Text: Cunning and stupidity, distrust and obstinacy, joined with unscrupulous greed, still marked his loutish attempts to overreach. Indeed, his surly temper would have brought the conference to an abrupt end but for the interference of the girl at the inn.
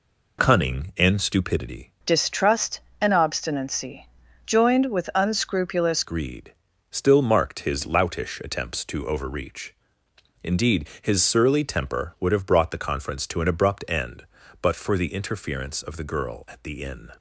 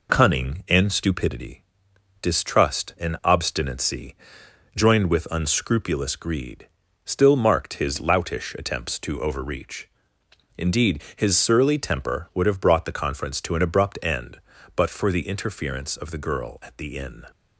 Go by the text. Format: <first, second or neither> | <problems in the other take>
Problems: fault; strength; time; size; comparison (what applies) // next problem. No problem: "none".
second | changes voice from "distrust" to "unscrupulous"; from 2.0 to 6.0 s; 4.0 s long